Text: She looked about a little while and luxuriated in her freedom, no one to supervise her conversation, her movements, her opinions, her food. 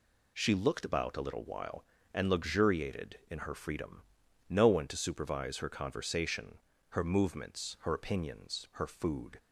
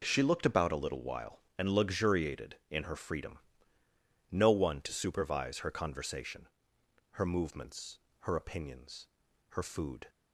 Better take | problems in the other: neither | none

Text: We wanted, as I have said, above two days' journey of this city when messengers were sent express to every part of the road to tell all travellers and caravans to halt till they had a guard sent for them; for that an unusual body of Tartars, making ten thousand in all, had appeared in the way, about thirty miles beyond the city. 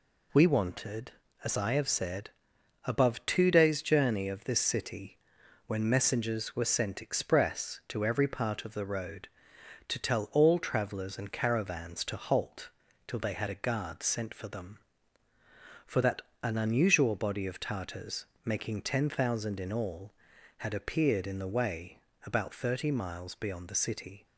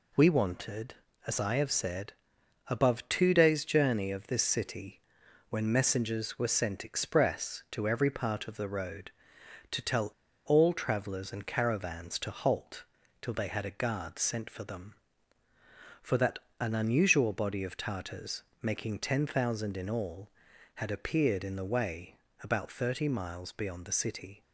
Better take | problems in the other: first | pauses between "city" and "when"; noticeable; at 5.0 s; 0.48 s long; noticeable in the first // pauses between "tell" and "all"; slight; at 10.1 s; 0.34 s long // pauses between "halt" and "till"; at 12.8 s; 0.38 s long; also in the first // pauses between "that" and "an"; slight; at 16.3 s; 0.22 s long; slight in the first

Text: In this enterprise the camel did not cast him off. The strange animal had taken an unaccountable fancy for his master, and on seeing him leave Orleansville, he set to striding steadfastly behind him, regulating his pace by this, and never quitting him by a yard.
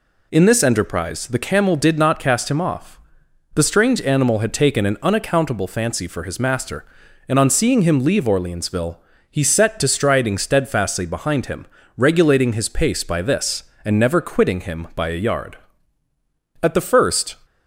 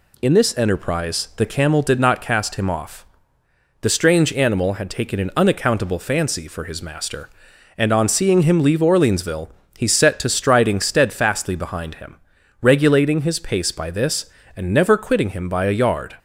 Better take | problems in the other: second | goes on to say "At the first"; noticeable; from 16.6 s on; 0.74 s long

